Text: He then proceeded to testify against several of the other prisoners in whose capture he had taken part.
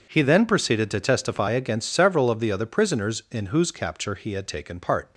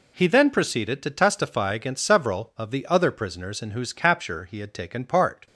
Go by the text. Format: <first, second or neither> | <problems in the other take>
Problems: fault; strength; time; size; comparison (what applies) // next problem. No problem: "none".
neither | none